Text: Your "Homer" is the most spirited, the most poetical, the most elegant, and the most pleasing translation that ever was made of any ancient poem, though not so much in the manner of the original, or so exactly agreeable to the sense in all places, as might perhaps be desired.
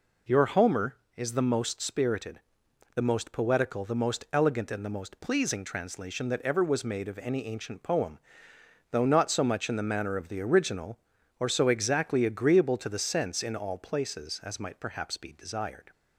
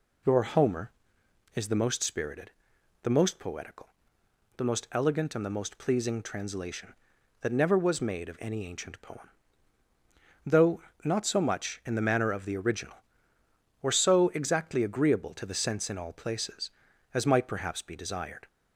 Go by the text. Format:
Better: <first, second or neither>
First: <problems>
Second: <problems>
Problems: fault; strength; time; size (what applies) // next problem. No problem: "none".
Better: first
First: none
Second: says "never" for "ever"; at 7.5 s // pauses between "though" and "not"; slight; at 10.8 s; 0.22 s long